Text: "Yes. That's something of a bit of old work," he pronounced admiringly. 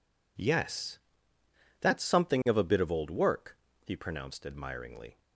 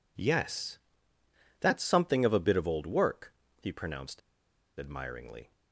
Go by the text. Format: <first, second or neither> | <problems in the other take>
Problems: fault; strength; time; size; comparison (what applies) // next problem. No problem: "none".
first | pauses between "pronounced" and "admiringly"; noticeable; at 4.2 s; 0.59 s long